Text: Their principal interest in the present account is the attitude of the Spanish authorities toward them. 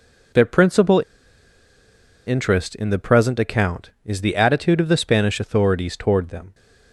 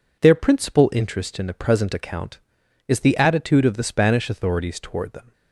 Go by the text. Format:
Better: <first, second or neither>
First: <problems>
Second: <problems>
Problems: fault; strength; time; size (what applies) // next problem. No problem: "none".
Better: second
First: pauses between "principal" and "interest"; at 1.0 s; 1.2 s long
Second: none